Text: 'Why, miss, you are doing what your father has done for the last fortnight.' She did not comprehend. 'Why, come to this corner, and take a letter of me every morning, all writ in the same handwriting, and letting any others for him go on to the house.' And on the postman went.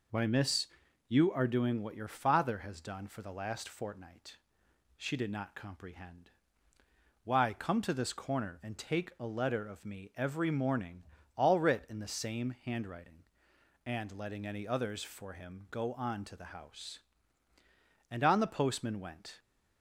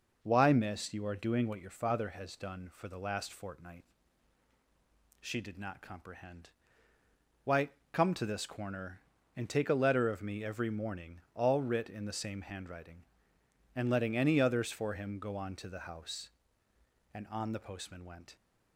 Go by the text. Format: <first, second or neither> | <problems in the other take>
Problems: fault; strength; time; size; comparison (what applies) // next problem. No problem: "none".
neither | none